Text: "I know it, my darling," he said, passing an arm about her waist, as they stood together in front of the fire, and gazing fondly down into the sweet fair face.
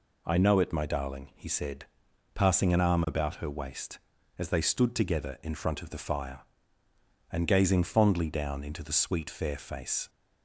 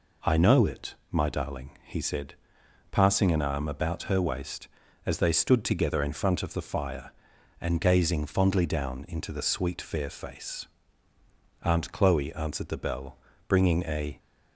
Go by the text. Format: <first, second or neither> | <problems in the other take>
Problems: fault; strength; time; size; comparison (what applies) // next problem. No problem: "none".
first | goes on to say "Aunt Chloe answered the bell bringing a"; strong; from 11.6 s on; 2.5 s long